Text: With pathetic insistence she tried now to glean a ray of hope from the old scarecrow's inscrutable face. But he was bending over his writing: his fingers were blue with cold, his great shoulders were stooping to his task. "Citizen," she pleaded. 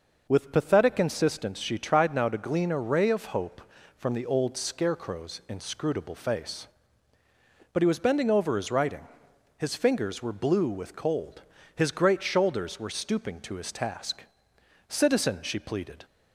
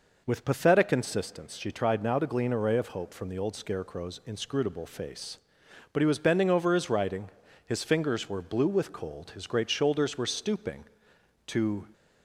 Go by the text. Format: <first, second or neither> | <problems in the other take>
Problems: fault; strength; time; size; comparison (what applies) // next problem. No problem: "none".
first | stops before "his task Citizen she pleaded"; at 11.9 s